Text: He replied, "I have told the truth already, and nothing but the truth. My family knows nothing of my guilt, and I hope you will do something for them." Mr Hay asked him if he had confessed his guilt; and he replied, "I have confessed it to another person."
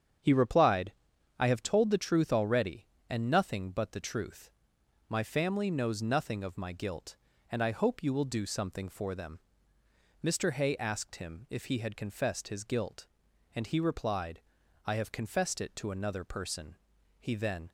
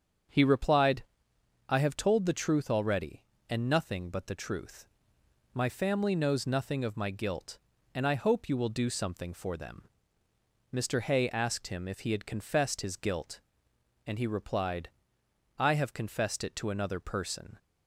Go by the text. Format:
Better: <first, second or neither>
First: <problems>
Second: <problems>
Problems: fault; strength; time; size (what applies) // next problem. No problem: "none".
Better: second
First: starts louder than the rest; strong; until 1.6 s; 8 dB // goes on to say "He then"; from 17.2 s on; 0.50 s long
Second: starts louder than the rest; strong; until 1.9 s; 7.5 dB